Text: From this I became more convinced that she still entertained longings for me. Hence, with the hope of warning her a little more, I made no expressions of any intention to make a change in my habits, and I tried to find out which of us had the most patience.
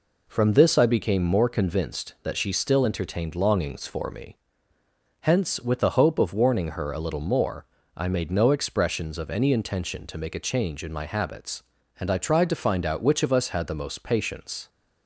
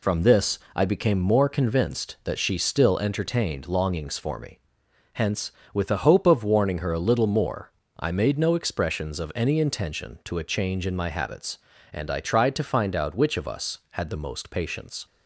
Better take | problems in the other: first | pauses between "this" and "I"; slight; at 0.5 s; 0.16 s long // skips "make"; at 10.3 s

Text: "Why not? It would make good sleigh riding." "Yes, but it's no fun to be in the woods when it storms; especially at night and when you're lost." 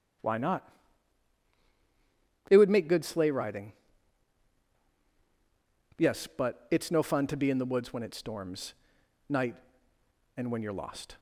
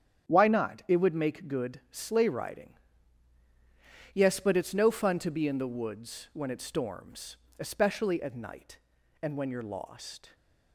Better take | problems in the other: second | starts louder than the rest; strong; until 3.0 s; 10 dB; strong in the second // skips "especially at"; at 9.0 s

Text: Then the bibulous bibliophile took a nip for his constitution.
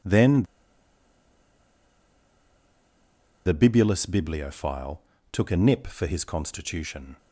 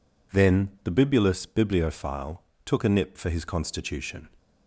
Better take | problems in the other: second | pauses between "Then" and "the"; strong; at 0.4 s; 3.0 s long // pauses between "bibliophile" and "took"; slight; at 5.0 s; 0.32 s long; slight in the second

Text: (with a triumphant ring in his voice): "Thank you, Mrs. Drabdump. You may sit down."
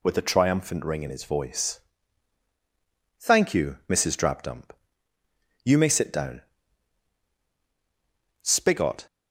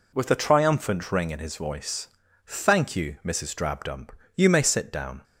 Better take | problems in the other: second | goes on to say "SPIGOT"; noticeable; from 8.4 s on; 0.64 s long

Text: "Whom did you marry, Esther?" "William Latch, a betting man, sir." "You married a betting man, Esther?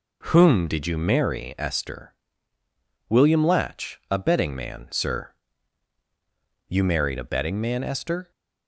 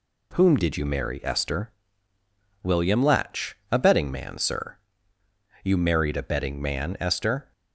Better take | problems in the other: neither | none

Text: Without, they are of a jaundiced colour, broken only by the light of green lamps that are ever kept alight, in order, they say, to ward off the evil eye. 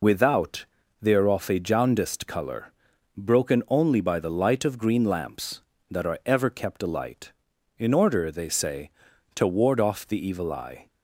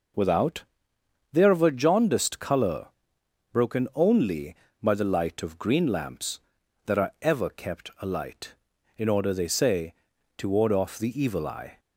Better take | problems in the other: second | loses the start of "Without"; at 0.0 s; 55 ms

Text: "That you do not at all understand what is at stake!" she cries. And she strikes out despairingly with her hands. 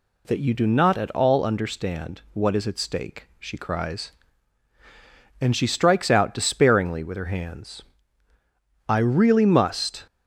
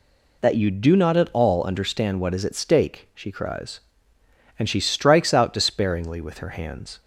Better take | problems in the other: second | goes on to say "I really must"; noticeable; from 8.8 s on; 1.1 s long

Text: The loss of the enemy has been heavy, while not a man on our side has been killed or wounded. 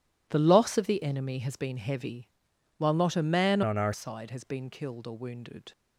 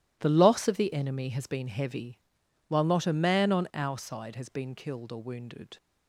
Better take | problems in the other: second | changes voice from "on" to "our"; from 3.6 to 3.9 s; 0.3 s long

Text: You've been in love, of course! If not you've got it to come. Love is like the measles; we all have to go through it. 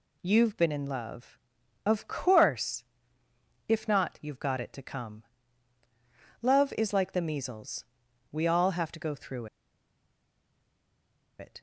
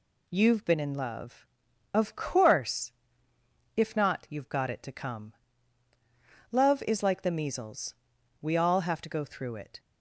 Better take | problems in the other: second | pauses between "through" and "it"; strong; at 9.4 s; 1.9 s long

